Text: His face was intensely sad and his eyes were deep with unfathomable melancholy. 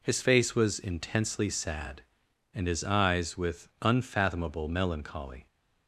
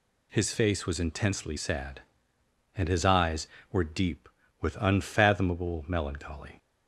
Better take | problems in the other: second | skips "were deep"; at 3.3 s

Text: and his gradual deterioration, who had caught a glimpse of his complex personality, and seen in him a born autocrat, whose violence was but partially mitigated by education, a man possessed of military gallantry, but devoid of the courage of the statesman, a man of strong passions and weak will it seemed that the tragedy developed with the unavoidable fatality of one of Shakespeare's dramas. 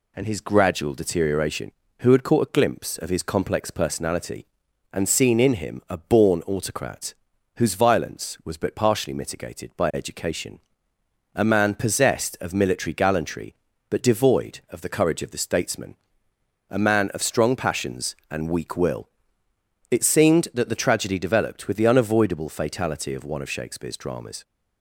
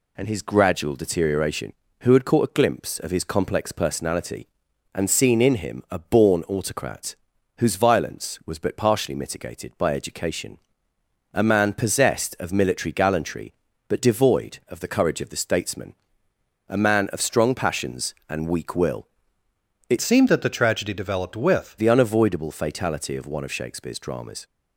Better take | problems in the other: first | pauses between "will" and "it"; noticeable; at 19.0 s; 0.80 s long; noticeable in the first // changes voice from "seemed" to "with"; from 20.0 to 21.7 s; 1.7 s long

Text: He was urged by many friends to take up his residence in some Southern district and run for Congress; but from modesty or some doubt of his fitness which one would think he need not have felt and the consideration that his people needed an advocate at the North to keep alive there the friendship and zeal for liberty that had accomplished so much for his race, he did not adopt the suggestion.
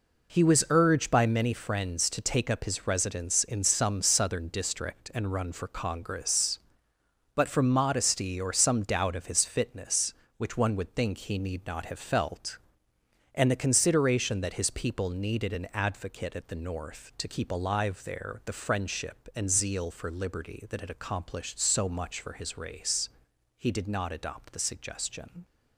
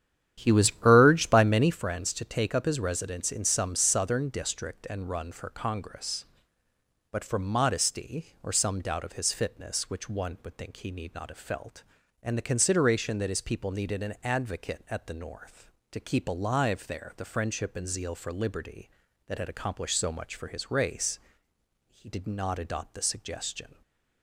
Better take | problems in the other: first | starts louder than the rest; strong; until 1.8 s; 10.5 dB

